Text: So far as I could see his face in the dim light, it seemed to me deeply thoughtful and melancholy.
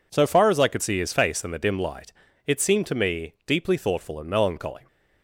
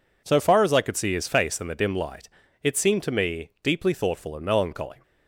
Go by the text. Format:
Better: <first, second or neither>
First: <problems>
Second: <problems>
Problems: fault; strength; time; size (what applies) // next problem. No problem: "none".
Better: neither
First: none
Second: none